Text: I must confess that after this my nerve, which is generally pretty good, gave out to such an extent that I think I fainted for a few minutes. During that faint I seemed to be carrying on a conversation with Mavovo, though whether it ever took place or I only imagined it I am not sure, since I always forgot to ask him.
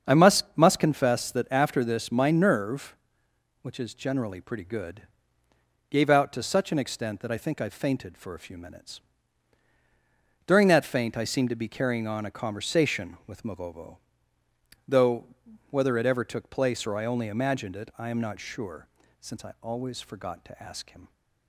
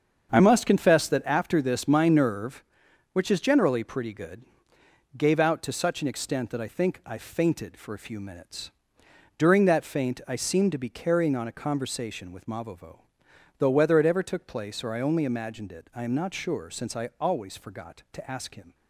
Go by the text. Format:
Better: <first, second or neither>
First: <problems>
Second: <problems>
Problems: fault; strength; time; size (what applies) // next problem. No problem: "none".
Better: second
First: starts louder than the rest; strong; until 1.1 s; 7 dB // says "must" twice; at 0.5 s // pauses between "though" and "whether"; noticeable; at 15.2 s; 0.46 s long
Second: starts louder than the rest; until 1.3 s; 7 dB